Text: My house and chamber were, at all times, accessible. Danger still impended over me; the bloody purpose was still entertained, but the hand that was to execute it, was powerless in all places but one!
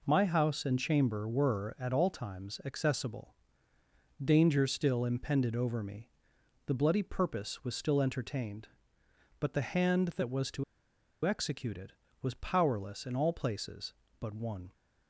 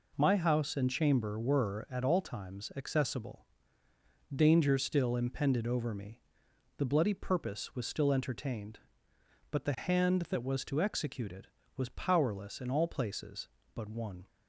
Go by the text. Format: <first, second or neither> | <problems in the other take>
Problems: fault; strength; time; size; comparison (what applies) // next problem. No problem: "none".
second | pauses between "to" and "execute"; noticeable; at 10.6 s; 0.61 s long